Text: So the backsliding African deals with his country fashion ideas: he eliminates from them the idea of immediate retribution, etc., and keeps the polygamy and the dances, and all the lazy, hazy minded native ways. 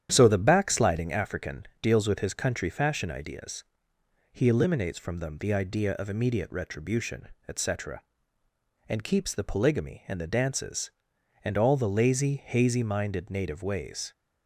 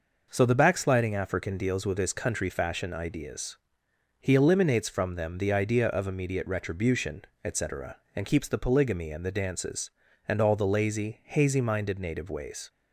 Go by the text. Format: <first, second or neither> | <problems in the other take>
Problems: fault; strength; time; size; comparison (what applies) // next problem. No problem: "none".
second | starts louder than the rest; strong; until 1.2 s; 10 dB